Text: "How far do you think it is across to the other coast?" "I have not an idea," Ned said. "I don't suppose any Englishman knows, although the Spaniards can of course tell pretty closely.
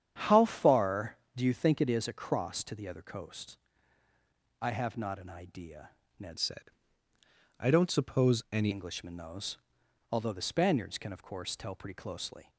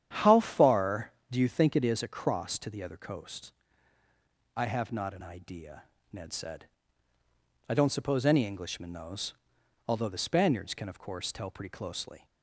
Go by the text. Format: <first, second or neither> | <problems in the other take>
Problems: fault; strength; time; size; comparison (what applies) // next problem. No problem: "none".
second | starts louder than the rest; strong; until 1.1 s; 9 dB; strong in the second // changes voice from "said" to "any"; from 6.3 to 8.6 s; 2.3 s long